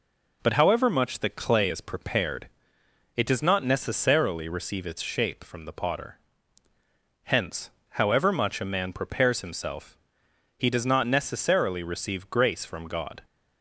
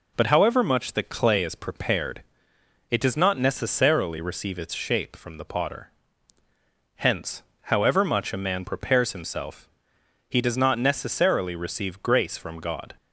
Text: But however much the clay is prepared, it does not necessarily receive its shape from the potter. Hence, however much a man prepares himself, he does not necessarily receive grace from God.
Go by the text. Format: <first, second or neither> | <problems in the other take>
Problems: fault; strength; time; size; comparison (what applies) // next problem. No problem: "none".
neither | none